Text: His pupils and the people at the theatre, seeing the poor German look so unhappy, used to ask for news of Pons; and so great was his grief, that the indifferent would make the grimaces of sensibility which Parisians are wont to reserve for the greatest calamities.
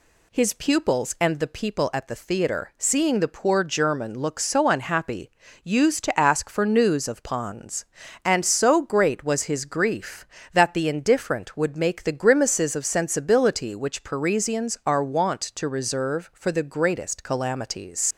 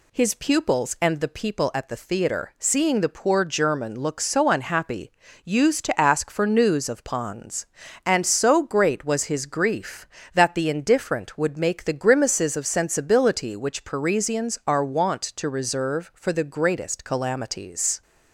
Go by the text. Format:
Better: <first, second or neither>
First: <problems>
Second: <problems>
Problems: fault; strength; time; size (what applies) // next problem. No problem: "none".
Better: second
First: leaves "calamities" unfinished; at 18.1 s; 100 ms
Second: none